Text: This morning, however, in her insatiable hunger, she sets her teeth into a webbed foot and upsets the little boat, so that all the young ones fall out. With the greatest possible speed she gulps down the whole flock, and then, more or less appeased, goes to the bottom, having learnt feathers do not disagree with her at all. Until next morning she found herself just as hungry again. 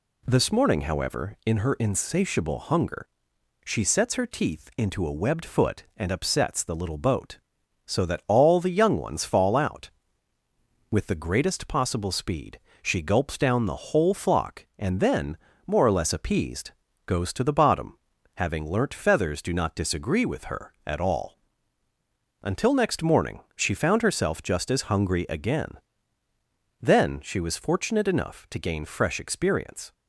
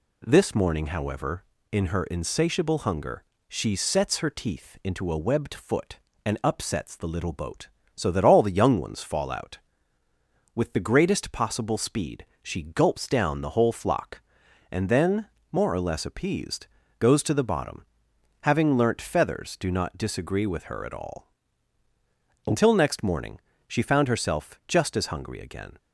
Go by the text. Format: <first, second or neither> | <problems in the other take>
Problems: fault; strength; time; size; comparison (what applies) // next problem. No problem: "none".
second | pauses between "speed" and "she"; slight; at 12.5 s; 0.22 s long; slight in the second // pauses between "morning" and "she"; slight; at 23.4 s; 0.16 s long; slight in the second // goes on to say "Then she was fortunate enough to gain fresh experience"; strong; from 26.8 s on; 3.1 s long